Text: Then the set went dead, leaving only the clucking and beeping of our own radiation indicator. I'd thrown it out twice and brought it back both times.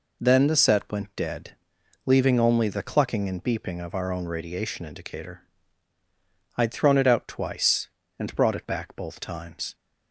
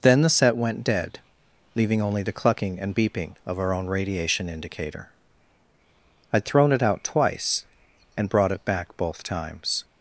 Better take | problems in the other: neither | none

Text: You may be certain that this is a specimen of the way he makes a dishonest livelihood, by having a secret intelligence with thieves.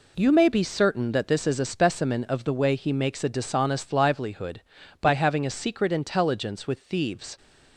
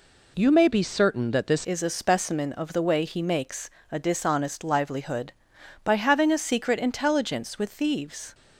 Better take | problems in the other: first | changes voice at "is"; from 1.6 s on; 6.7 s long // pauses between "makes" and "a"; slight; at 3.7 s; 0.20 s long

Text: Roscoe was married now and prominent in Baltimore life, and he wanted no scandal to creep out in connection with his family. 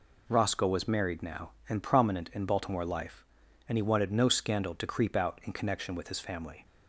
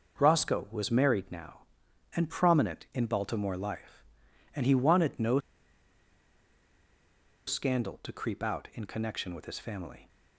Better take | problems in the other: first | pauses between "no" and "scandal"; strong; at 5.3 s; 2.0 s long

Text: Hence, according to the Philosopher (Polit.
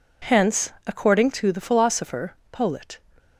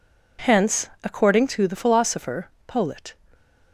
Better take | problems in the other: neither | none

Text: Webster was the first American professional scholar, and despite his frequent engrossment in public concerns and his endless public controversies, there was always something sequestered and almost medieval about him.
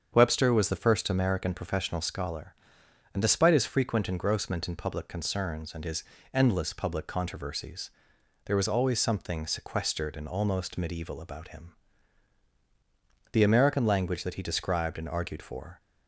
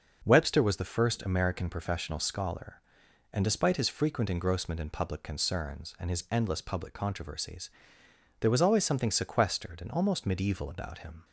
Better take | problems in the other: second | starts louder than the rest; strong; until 1.1 s; 7 dB // pauses between "his" and "endless"; slight; at 6.0 s; 0.28 s long // goes on to say "The American language that he described and argued for"; strong; from 13.3 s on; 2.4 s long

